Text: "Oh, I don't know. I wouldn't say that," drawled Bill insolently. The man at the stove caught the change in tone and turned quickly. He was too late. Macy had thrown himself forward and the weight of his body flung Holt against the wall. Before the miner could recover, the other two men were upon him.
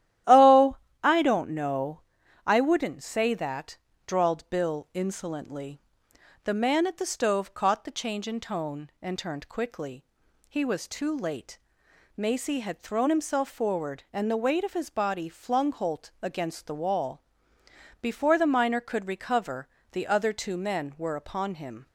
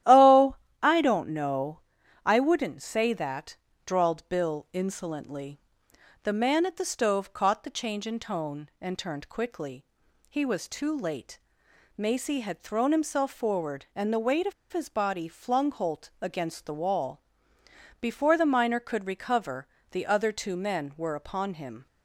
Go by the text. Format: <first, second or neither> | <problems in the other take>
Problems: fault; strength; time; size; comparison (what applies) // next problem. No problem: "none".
first | starts louder than the rest; strong; until 1.3 s; 13 dB; strong in the first // pauses between "of" and "his"; slight; at 14.5 s; 0.19 s long